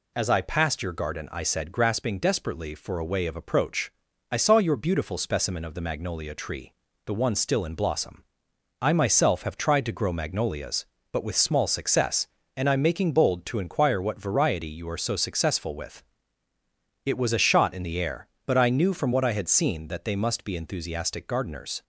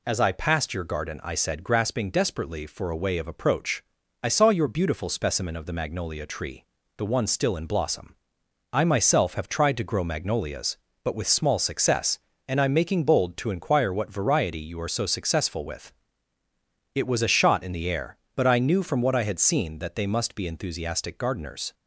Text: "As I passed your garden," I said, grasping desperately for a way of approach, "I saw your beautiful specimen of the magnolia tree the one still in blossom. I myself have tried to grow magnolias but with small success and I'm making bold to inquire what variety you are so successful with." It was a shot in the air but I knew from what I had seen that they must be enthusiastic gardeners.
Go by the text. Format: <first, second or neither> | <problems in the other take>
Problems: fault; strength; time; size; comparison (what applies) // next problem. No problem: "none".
neither | pauses between "tree" and "the"; slight; the same in both